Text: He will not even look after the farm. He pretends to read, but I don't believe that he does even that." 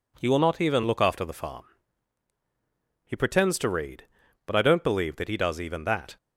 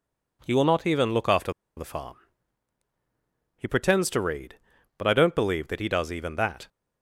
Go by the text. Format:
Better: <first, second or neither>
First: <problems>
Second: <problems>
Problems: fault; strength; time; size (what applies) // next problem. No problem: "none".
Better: first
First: none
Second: pauses between "after" and "the"; slight; at 1.5 s; 0.24 s long